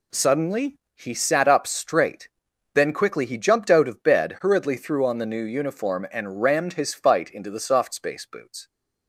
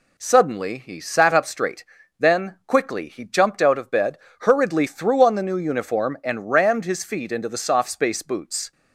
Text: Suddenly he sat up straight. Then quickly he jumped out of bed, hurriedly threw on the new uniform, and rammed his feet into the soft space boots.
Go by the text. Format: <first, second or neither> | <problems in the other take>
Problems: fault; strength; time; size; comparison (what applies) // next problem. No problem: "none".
second | pauses between "Suddenly" and "he"; slight; at 0.7 s; 0.20 s long // says "fight" for "feet"; at 6.9 s